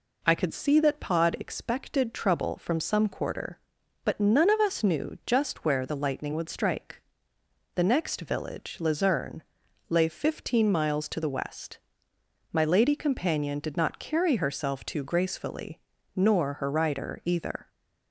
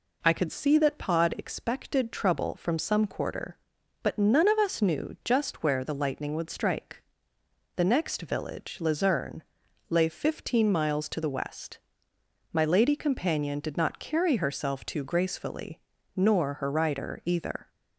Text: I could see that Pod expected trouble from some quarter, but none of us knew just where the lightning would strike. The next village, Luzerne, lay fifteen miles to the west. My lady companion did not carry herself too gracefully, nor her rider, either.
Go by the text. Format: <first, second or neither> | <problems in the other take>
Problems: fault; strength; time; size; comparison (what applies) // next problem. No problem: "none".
neither | none